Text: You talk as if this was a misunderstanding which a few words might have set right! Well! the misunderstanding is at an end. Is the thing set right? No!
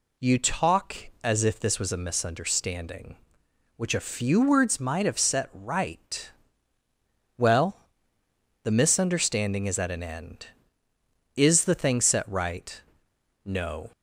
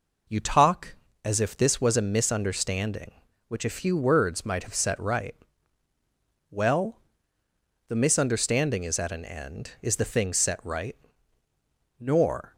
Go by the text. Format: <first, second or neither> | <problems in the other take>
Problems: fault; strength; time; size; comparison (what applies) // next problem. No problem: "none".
first | says "Nor" for "No"; at 11.9 s